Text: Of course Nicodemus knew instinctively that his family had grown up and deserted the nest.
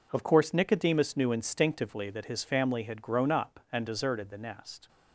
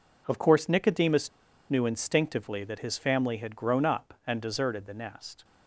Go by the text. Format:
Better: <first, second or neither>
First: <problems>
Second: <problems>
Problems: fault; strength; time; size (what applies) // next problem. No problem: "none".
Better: first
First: none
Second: pauses between "Nicodemus" and "knew"; at 1.3 s; 0.39 s long